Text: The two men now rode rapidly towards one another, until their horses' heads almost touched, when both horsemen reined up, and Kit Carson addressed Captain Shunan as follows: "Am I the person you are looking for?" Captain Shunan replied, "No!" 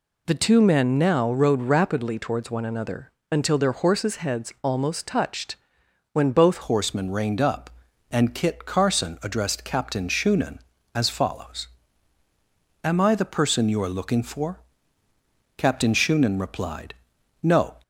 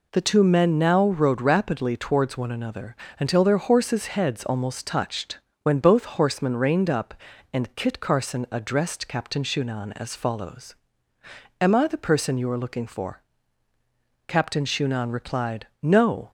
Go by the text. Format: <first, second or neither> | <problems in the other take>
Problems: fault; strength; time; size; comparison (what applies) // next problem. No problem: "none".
second | changes voice at "horsemen"; from 6.6 s on; 11.1 s long